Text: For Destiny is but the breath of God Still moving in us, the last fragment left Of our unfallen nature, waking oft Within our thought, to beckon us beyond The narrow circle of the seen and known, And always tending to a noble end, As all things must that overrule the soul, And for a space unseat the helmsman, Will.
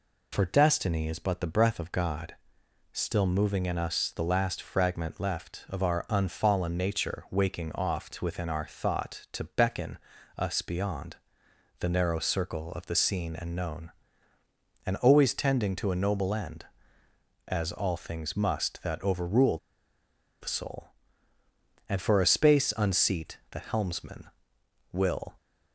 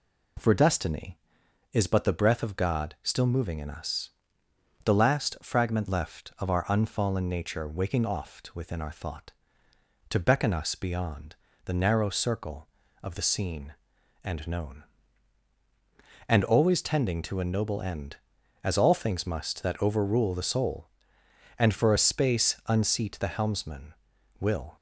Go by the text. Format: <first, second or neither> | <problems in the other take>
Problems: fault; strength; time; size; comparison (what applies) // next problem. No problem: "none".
second | pauses between "God" and "Still"; noticeable; at 2.3 s; 0.58 s long // pauses between "beckon" and "us"; slight; at 9.9 s; 0.36 s long // pauses between "beyond" and "The"; noticeable; at 11.1 s; 0.60 s long; slight in the second // pauses between "overrule" and "the"; noticeable; at 19.5 s; 0.83 s long